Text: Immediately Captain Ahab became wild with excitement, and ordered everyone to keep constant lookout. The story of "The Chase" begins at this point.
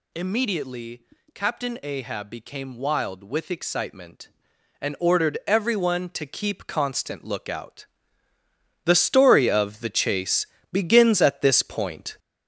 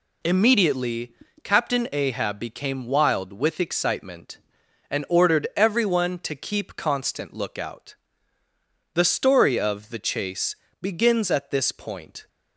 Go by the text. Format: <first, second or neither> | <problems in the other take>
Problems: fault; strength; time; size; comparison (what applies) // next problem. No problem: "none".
second | gets louder; noticeable; throughout; 5.5 dB // pauses between "Immediately" and "Captain"; slight; at 1.0 s; 0.30 s long; slight in the second // pauses between "Chase" and "begins"; slight; at 10.4 s; 0.26 s long; slight in the second